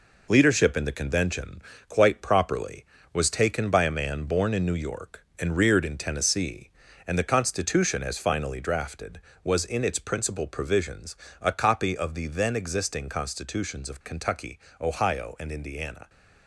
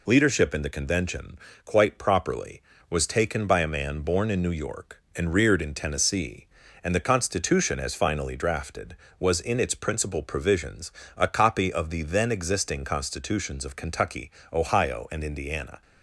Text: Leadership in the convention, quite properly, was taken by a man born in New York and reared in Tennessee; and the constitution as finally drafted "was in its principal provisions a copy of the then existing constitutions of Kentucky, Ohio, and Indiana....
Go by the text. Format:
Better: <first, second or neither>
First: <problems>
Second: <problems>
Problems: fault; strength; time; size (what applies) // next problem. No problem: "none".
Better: second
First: gets quieter; noticeable; throughout; 6 dB // pauses between "provisions" and "a"; slight; at 11.1 s; 0.26 s long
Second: pauses between "provisions" and "a"; slight; at 10.9 s; 0.26 s long